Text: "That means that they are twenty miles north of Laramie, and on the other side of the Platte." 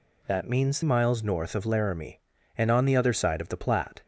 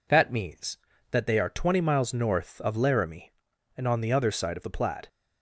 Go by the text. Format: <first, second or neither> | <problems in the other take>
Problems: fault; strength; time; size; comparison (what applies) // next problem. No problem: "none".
second | skips "that they are twenty"; at 0.8 s